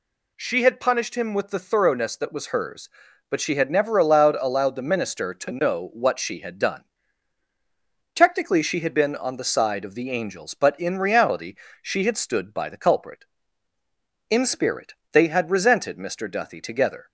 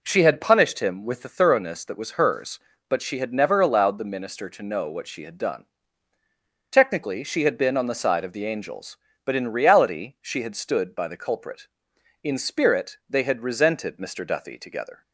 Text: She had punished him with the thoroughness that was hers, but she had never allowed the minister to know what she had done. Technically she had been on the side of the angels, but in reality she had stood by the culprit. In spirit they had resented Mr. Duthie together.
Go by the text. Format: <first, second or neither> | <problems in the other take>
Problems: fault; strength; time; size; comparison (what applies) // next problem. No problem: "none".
second | says "allowed" twice; at 4.3 s // pauses between "reality" and "she"; slight; at 11.5 s; 0.26 s long // pauses between "spirit" and "they"; slight; at 14.9 s; 0.18 s long